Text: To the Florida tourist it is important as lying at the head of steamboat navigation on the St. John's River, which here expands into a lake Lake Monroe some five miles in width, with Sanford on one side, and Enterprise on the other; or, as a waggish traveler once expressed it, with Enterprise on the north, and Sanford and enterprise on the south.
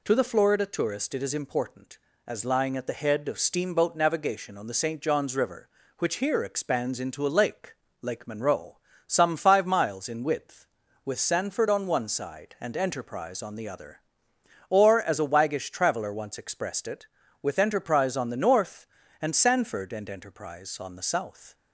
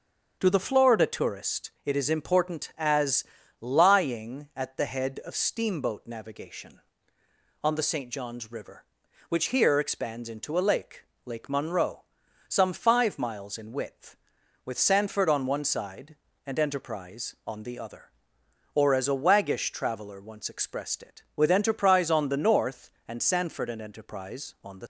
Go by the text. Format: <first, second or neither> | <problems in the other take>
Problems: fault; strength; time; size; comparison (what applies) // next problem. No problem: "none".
first | starts louder than the rest; until 1.4 s; 7 dB // pauses between "as" and "lying"; slight; at 3.2 s; 0.36 s long // pauses between "lake" and "Lake"; slight; at 11.0 s; 0.20 s long; slight in the first // pauses between "Monroe" and "some"; noticeable; at 12.0 s; 0.46 s long; slight in the first // stops before "south"; at 24.8 s